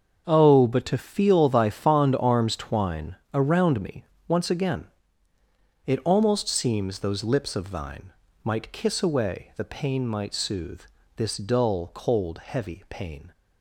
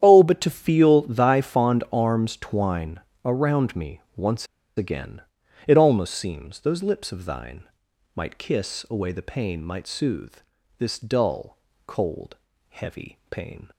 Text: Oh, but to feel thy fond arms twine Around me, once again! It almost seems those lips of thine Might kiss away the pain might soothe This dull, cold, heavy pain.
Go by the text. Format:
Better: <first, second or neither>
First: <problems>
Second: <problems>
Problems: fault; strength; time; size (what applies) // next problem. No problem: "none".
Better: first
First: starts louder than the rest; until 1.2 s; 6.5 dB // pauses between "twine" and "Around"; slight; at 3.1 s; 0.18 s long // pauses between "thine" and "Might"; slight; at 8.1 s; 0.32 s long // pauses between "soothe" and "This"; slight; at 10.8 s; 0.34 s long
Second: starts louder than the rest; strong; until 1.0 s; 9.5 dB // pauses between "twine" and "Around"; slight; at 3.0 s; 0.22 s long // pauses between "once" and "again"; slight; at 4.4 s; 0.31 s long // pauses between "thine" and "Might"; noticeable; at 7.6 s; 0.50 s long // pauses between "soothe" and "This"; at 10.3 s; 0.44 s long